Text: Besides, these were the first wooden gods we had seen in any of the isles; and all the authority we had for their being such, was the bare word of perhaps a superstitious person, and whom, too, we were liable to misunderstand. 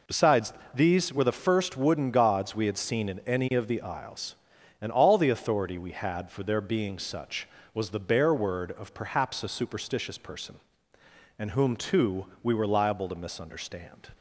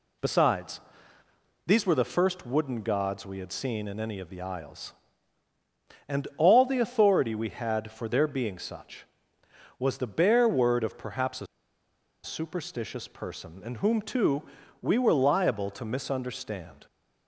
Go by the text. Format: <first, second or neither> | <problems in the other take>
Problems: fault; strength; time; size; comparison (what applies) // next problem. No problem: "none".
first | pauses between "a" and "superstitious"; noticeable; at 11.4 s; 0.77 s long